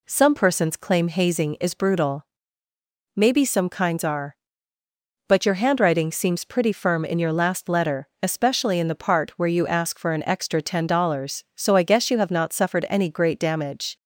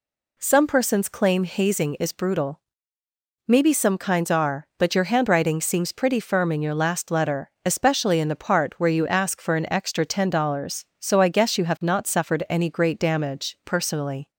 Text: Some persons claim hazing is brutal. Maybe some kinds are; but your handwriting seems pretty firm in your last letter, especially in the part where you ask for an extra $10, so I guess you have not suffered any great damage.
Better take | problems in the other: first | goes on to say "Personally"; noticeable; from 13.6 s on; 0.64 s long

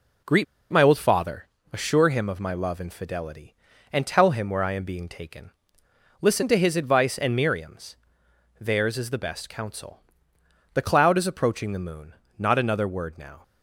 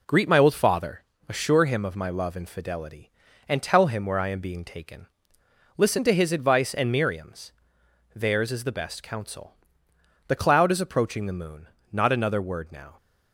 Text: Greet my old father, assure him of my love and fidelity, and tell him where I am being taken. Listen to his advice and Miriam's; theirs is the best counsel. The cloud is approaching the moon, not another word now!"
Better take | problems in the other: second | pauses between "Greet" and "my"; slight; at 0.4 s; 0.27 s long

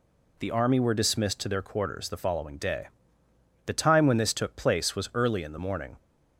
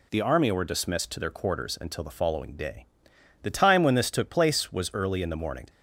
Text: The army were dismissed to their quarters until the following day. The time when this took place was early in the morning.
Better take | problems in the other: second | skips "until"; at 2.0 s

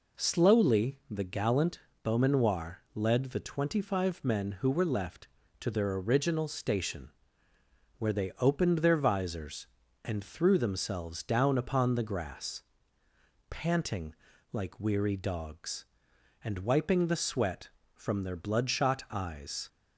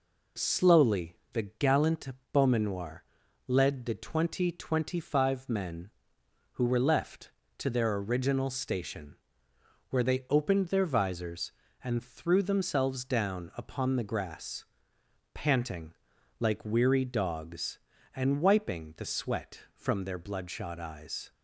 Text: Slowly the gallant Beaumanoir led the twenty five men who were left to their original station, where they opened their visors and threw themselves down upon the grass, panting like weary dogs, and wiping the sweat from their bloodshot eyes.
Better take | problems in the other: first | pauses between "Slowly" and "the"; slight; at 1.1 s; 0.18 s long // pauses between "gallant" and "Beaumanoir"; slight; at 2.0 s; 0.24 s long; slight in the first // pauses between "Beaumanoir" and "led"; at 3.0 s; 0.44 s long // says "twenty" twice; at 4.5 s // pauses between "panting" and "like"; at 15.9 s; 0.44 s long; also in the first

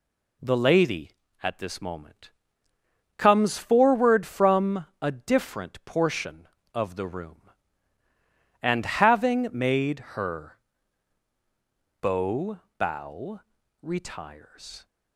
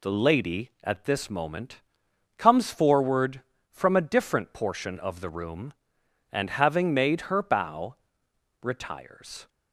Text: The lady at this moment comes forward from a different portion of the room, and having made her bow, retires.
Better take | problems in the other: second | pauses between "moment" and "comes"; noticeable; at 2.3 s; 0.86 s long; noticeable in the second // pauses between "from" and "a"; slight; at 4.8 s; 0.16 s long // pauses between "made" and "her"; slight; at 9.9 s; 0.16 s long // pauses between "her" and "bow"; strong; at 10.5 s; 1.4 s long // says "bow" twice; at 12.7 s

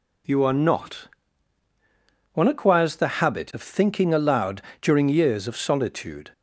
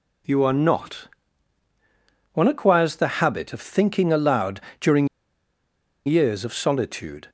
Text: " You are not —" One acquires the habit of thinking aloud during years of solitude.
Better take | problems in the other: first | pauses between "aloud" and "during"; slight; at 4.5 s; 0.20 s long; slight in the first // pauses between "during" and "years"; at 5.0 s; 1.0 s long

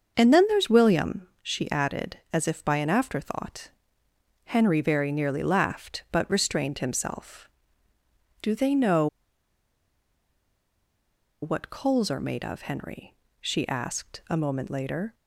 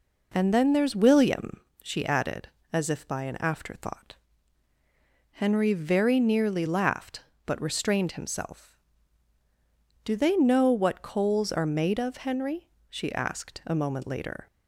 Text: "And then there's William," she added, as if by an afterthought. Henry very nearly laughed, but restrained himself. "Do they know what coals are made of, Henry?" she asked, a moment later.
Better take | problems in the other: second | starts louder than the rest; until 1.1 s; 6.5 dB // pauses between "know" and "what"; strong; at 9.0 s; 2.3 s long

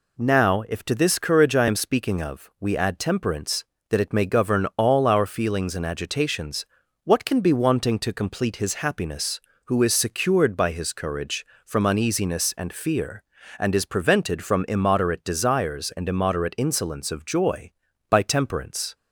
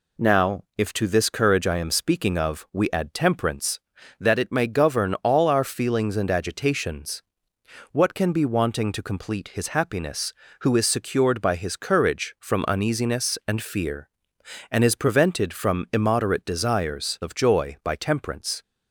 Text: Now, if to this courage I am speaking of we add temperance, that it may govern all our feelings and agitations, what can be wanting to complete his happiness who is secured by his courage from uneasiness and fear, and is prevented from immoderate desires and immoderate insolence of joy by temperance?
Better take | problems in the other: first | skips "and immoderate insolence"; at 17.1 s

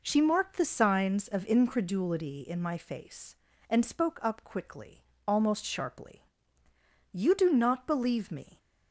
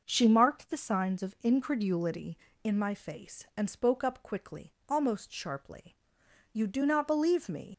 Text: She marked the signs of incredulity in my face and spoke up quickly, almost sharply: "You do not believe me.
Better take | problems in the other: first | starts louder than the rest; noticeable; until 1.0 s; 6 dB // leaves "me" unfinished; at 7.7 s; 100 ms

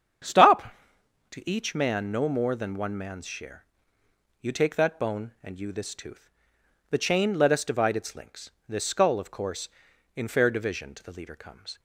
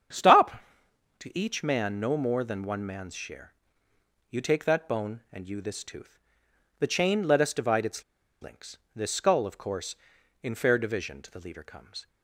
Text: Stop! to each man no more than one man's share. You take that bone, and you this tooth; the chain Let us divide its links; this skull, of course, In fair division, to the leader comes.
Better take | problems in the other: first | starts louder than the rest; strong; until 1.8 s; 8 dB; strong in the first // pauses between "its" and "links"; at 8.0 s; 0.38 s long

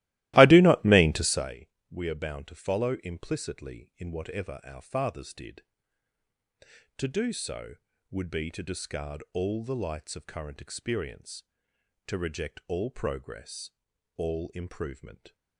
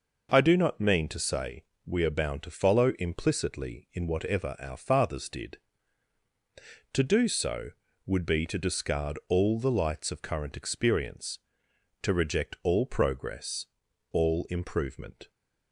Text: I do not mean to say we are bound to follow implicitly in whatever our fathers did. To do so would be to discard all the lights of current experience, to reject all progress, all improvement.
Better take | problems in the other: second | starts louder than the rest; strong; until 1.5 s; 17 dB // pauses between "say" and "we"; slight; at 1.6 s; 0.20 s long; slight in the second

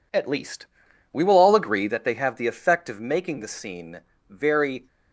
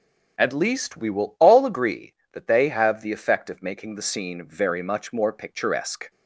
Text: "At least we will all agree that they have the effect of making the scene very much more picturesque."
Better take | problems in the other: second | pauses between "least" and "we"; noticeable; at 0.6 s; 0.48 s long // pauses between "scene" and "very"; slight; at 4.0 s; 0.26 s long // stops before "much more picturesque"; at 4.8 s

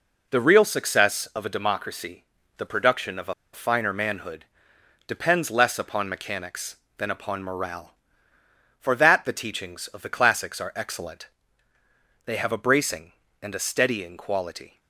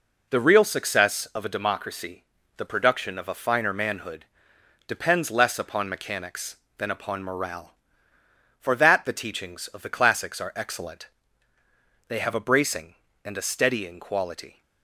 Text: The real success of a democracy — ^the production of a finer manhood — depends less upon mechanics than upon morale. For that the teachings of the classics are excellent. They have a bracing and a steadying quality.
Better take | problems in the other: second | pauses between "a" and "finer"; slight; at 3.3 s; 0.19 s long

